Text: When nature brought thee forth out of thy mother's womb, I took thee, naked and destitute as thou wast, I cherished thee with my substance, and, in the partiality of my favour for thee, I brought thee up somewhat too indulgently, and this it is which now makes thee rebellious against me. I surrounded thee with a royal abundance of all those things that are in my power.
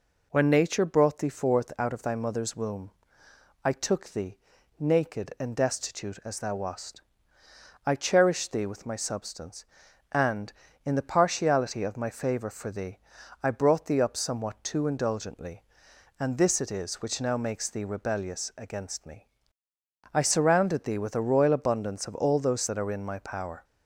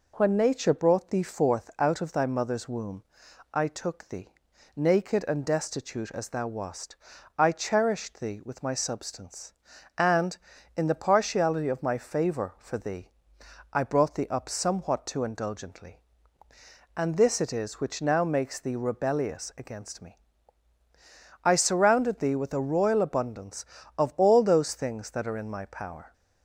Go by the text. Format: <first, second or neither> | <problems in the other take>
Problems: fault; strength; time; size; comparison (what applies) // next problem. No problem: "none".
second | skips "things"; at 22.6 s